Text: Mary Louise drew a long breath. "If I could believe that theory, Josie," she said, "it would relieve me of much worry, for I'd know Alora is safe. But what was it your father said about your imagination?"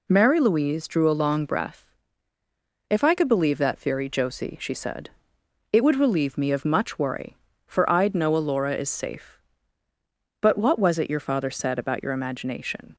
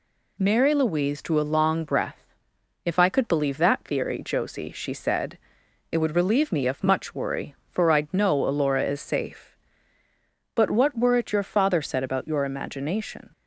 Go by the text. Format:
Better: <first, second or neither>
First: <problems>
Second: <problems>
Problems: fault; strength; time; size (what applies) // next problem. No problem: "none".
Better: first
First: none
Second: says "were" for "was"; at 10.9 s